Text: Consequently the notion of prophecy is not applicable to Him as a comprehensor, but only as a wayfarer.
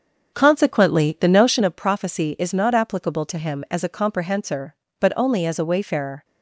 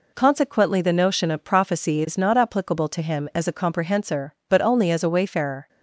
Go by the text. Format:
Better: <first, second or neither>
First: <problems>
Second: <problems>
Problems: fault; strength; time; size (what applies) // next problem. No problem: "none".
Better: second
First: starts louder than the rest; until 1.7 s; 6.5 dB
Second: none